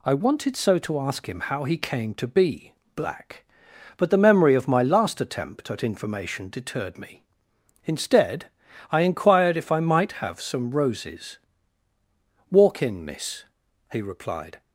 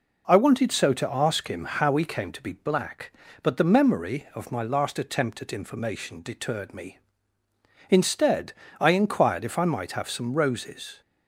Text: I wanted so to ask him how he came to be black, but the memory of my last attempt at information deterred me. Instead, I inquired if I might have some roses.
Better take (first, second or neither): second